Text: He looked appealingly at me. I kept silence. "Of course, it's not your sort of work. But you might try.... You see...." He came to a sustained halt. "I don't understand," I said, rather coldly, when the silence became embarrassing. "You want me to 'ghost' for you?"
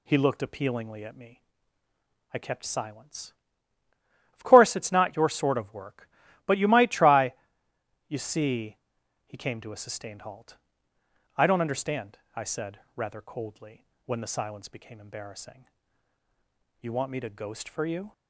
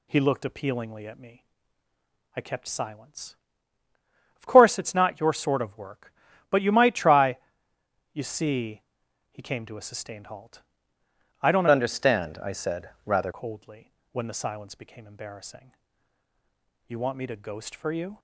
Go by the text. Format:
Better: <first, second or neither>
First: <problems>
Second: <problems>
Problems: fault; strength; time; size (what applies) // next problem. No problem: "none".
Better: first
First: none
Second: changes voice from "understand" to "rather"; from 11.7 to 13.3 s; 1.6 s long